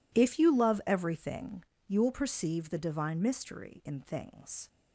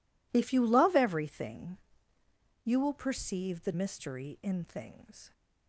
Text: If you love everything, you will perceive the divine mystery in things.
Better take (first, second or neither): first